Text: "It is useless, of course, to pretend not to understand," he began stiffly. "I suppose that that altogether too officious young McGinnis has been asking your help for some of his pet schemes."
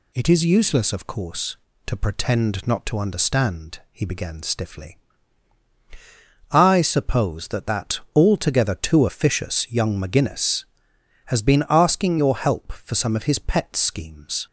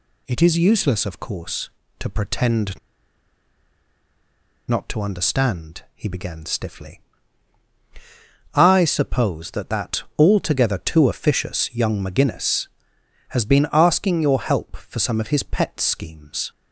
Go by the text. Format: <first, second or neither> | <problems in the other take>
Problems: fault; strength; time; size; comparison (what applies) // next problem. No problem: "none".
first | pauses between "pretend" and "not"; strong; at 2.7 s; 1.8 s long // pauses between "that" and "altogether"; slight; at 10.0 s; 0.16 s long; slight in the first